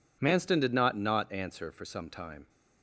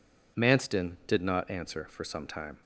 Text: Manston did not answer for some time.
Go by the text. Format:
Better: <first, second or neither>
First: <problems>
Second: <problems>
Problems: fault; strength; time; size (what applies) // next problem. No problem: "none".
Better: second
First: says "not" twice; at 0.9 s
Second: none